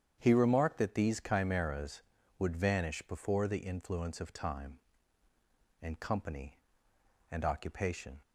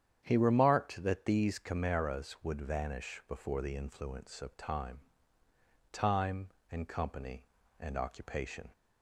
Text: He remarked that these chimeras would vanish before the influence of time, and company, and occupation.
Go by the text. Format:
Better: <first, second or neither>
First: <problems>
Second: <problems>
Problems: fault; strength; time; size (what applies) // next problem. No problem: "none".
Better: first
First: starts louder than the rest; strong; until 1.2 s; 8.5 dB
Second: starts louder than the rest; strong; until 1.2 s; 9 dB // says "time" twice; at 5.9 s